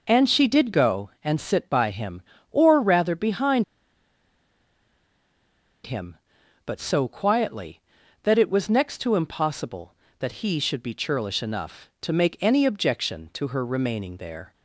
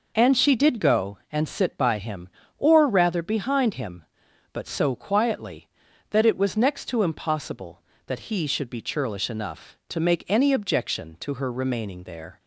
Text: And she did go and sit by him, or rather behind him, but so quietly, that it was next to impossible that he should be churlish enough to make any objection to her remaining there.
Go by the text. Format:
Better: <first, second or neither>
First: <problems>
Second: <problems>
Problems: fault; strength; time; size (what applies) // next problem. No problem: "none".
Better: second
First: pauses between "behind" and "him"; strong; at 3.6 s; 2.2 s long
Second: none